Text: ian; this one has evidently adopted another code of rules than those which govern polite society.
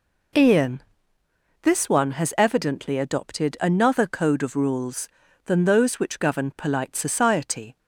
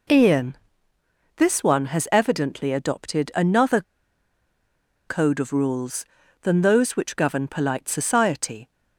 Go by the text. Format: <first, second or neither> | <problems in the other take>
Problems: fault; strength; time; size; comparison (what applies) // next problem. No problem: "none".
first | pauses between "another" and "code"; strong; at 3.8 s; 1.2 s long